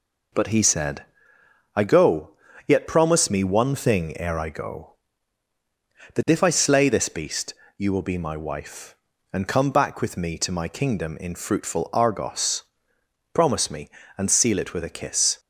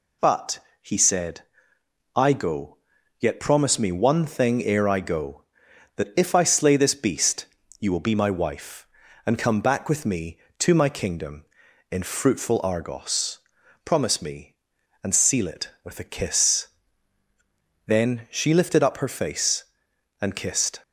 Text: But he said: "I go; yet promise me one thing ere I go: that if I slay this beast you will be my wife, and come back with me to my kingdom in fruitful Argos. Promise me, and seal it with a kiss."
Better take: first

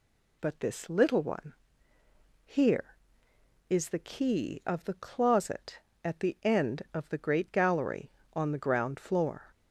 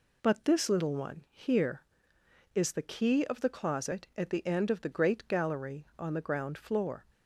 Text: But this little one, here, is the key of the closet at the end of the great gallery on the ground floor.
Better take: neither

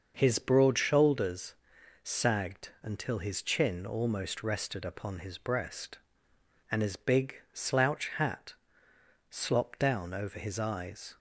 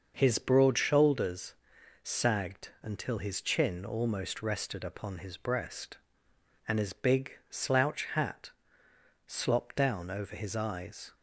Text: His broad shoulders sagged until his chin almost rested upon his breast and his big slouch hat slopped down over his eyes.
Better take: neither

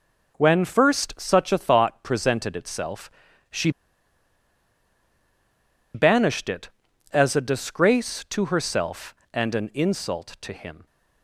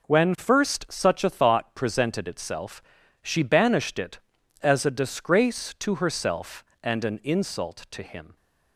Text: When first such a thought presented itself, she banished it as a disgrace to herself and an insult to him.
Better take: second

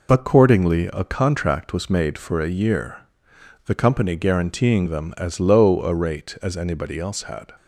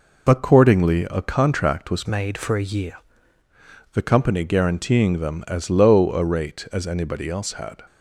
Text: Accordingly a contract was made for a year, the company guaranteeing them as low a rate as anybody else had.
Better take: first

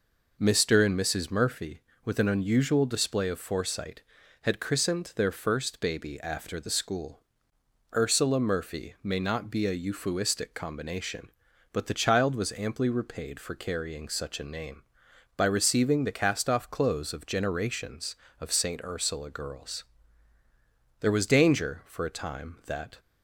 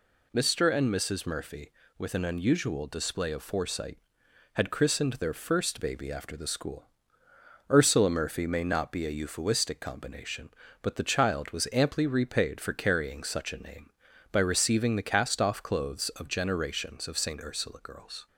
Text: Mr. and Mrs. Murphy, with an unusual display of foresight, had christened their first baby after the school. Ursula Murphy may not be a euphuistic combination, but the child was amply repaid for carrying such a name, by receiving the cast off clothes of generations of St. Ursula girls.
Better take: second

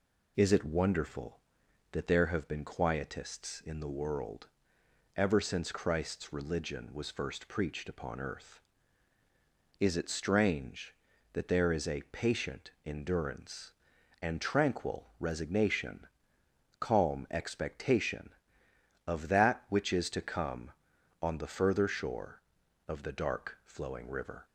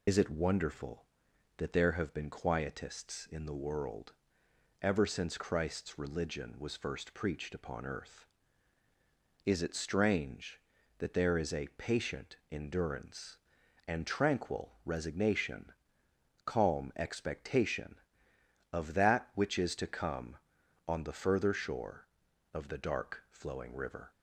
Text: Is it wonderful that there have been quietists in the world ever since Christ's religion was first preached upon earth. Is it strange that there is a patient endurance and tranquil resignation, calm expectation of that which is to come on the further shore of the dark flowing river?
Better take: first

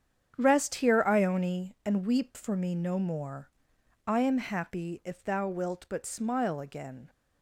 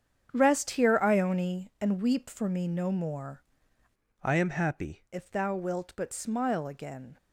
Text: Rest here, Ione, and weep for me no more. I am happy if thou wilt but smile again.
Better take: first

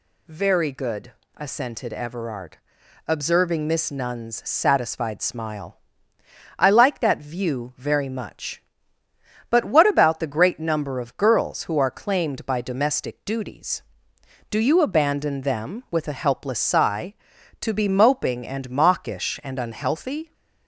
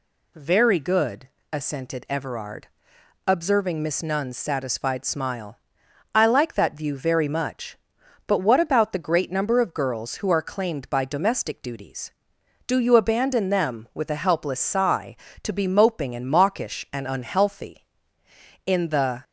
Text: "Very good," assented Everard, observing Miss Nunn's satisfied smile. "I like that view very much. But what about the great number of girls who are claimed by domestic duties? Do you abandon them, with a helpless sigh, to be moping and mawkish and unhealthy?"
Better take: first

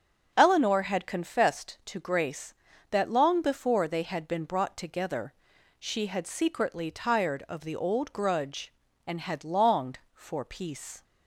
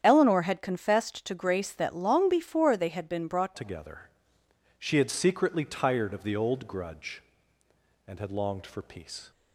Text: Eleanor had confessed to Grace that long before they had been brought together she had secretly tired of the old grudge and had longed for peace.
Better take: first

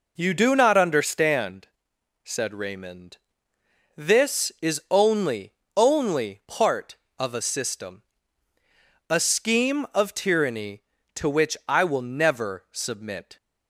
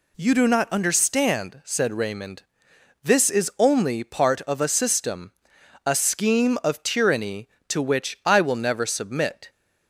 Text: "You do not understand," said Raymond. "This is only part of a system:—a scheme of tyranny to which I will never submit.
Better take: second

